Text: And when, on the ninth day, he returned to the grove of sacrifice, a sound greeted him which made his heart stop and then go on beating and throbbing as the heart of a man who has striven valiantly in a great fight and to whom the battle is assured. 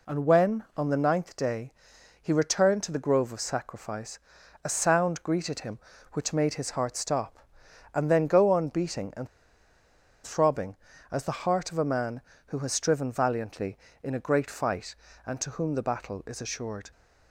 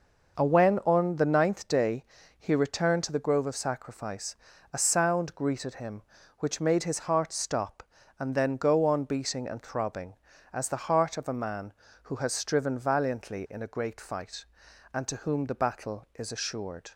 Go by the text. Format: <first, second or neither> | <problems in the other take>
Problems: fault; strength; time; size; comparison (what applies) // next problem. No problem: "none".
second | pauses between "and" and "throbbing"; at 9.2 s; 0.99 s long